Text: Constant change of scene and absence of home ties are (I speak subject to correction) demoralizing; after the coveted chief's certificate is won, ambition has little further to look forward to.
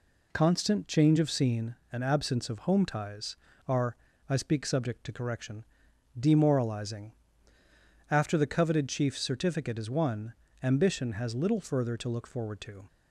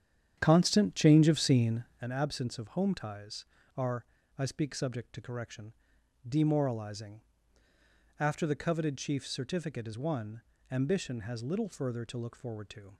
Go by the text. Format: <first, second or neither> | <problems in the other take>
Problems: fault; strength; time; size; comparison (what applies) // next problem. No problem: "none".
first | starts louder than the rest; strong; until 2.1 s; 9 dB